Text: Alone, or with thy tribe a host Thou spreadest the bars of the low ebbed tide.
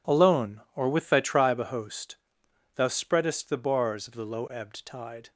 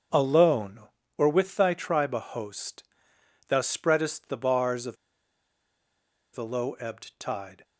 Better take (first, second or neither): first